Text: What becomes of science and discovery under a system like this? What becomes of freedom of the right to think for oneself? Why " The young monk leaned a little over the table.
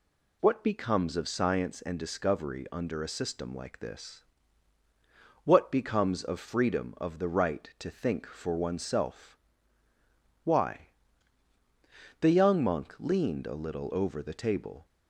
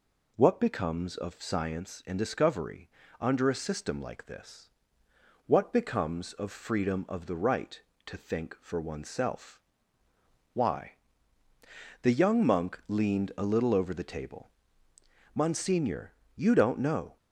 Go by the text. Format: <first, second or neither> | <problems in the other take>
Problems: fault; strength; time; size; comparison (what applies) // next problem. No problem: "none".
first | pauses between "discovery" and "under"; slight; at 2.8 s; 0.32 s long // goes on to say "Monsignor you don't know"; strong; from 15.3 s on; 1.8 s long